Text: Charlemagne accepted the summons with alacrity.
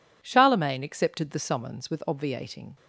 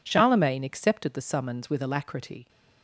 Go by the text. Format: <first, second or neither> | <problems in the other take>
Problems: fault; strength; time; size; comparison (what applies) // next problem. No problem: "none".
second | says "obviating" for "alacrity"; at 2.0 s